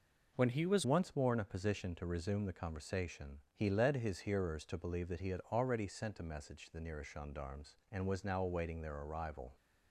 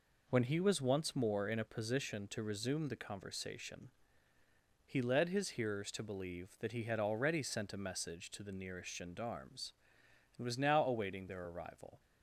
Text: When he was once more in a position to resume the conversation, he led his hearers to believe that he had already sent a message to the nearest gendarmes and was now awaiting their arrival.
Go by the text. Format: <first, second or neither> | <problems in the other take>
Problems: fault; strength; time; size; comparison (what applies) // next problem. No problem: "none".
second | changes voice at "once"; from 0.8 s on; 8.7 s long